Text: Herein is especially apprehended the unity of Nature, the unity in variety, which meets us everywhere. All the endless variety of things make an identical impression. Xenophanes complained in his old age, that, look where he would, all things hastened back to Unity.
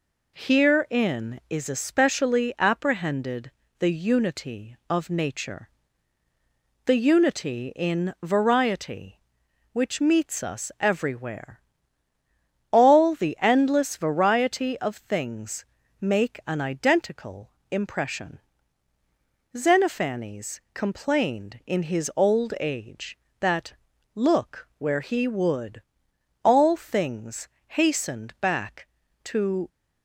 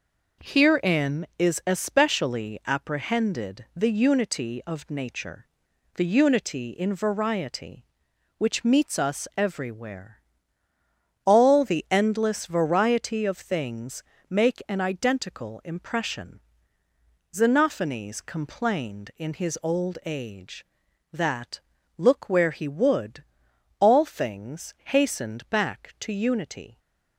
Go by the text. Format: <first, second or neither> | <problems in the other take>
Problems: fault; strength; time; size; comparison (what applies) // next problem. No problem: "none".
second | pauses between "apprehended" and "the"; slight; at 3.5 s; 0.26 s long // pauses between "things" and "make"; slight; at 15.6 s; 0.36 s long; slight in the second // pauses between "identical" and "impression"; slight; at 17.5 s; 0.20 s long // pauses between "things" and "hastened"; slight; at 27.4 s; 0.22 s long // stops before "Unity"; at 29.6 s